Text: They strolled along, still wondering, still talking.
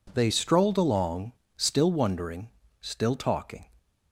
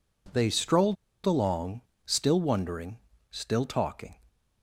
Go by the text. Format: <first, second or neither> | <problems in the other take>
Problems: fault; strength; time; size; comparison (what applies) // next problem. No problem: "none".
first | pauses between "strolled" and "along"; slight; at 0.9 s; 0.29 s long